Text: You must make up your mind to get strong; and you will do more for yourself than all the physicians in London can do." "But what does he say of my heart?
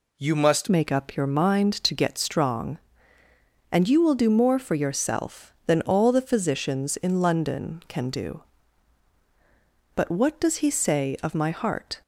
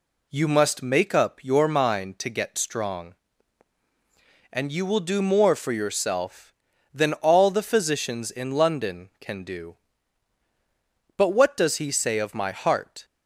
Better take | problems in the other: second | changes voice at "make"; from 0.6 s on; 11.4 s long

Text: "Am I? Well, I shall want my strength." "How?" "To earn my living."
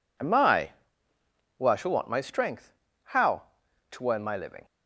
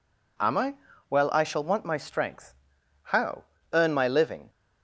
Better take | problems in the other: first | skips "To"; at 3.5 s

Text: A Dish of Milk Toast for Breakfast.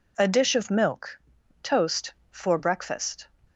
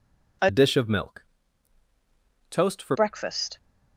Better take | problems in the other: first | changes voice from "Dish" to "for"; from 0.4 to 2.9 s; 2.5 s long // pauses between "Milk" and "Toast"; at 1.2 s; 1.2 s long; also in the first

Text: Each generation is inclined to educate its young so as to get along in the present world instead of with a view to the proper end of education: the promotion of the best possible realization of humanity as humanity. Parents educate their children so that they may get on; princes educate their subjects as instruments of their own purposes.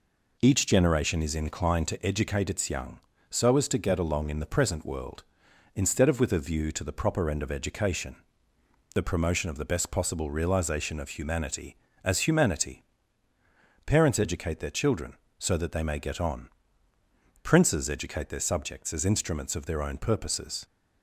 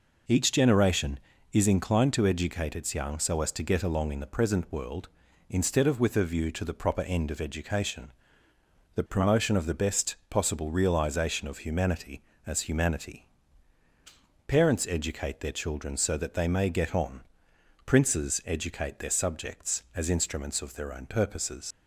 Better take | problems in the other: first | leaves "purposes" unfinished; at 21.7 s; 90 ms

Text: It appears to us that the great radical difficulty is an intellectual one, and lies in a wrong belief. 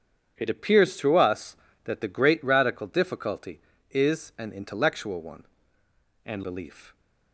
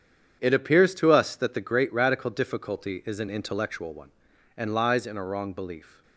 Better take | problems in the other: second | starts louder than the rest; strong; until 1.3 s; 8 dB; strong in the second // skips "lies in a wrong"; at 6.4 s

